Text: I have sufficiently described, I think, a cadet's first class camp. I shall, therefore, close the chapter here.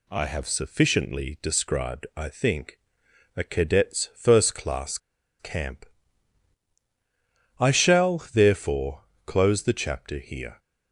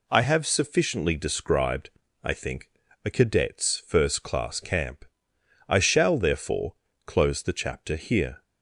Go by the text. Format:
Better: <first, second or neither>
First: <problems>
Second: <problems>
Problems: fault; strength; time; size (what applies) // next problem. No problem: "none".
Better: second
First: pauses between "class" and "camp"; at 4.9 s; 0.42 s long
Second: none